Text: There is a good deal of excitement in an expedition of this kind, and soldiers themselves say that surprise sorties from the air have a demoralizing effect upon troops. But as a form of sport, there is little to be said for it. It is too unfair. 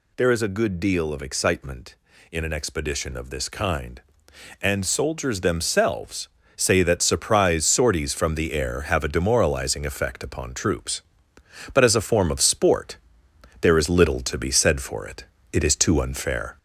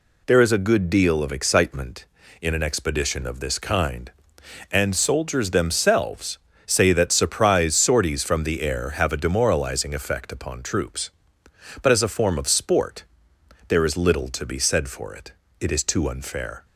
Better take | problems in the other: second | gets louder; slight; throughout; 3 dB // pauses between "themselves" and "say"; slight; at 6.2 s; 0.28 s long; slight in the second

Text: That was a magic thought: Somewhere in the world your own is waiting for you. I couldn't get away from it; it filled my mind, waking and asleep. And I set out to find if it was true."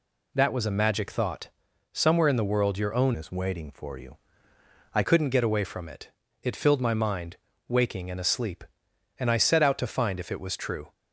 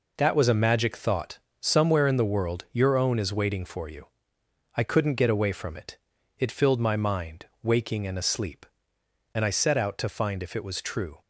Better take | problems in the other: second | changes voice from "is" to "I"; from 3.1 to 5.0 s; 1.9 s long

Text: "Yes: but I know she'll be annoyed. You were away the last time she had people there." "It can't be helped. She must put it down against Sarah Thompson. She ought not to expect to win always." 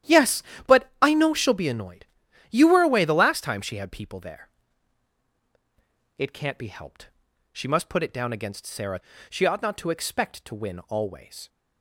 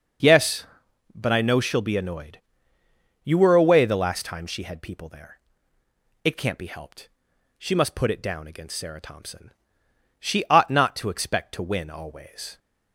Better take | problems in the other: second | starts louder than the rest; strong; until 1.3 s; 11.5 dB // skips "Thompson"; at 9.1 s

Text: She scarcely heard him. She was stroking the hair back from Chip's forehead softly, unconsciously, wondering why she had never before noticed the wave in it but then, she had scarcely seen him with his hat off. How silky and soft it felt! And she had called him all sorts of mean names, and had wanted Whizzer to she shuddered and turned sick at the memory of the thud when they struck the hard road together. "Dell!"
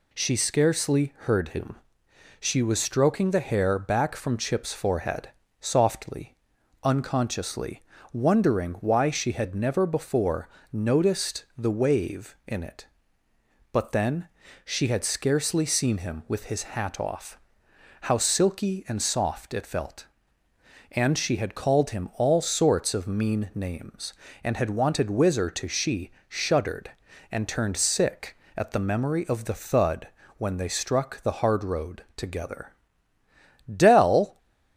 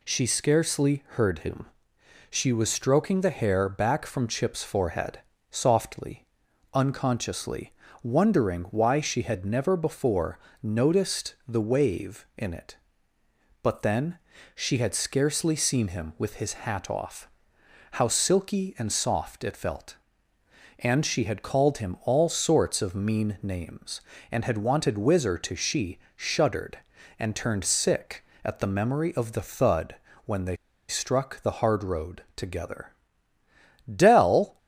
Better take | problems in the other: first | pauses between "forehead" and "softly"; slight; at 5.1 s; 0.30 s long; slight in the first // pauses between "before" and "noticed"; slight; at 10.3 s; 0.24 s long; slight in the first // pauses between "she" and "shuddered"; slight; at 25.9 s; 0.16 s long; slight in the first // pauses between "thud" and "when"; slight; at 29.9 s; 0.32 s long; slight in the first // pauses between "they" and "struck"; slight; at 30.5 s; 0.33 s long

